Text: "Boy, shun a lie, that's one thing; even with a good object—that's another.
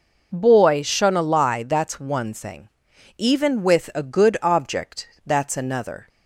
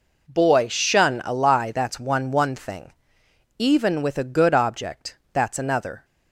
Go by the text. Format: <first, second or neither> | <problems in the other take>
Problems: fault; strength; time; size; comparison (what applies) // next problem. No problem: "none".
first | says "one" twice; at 2.3 s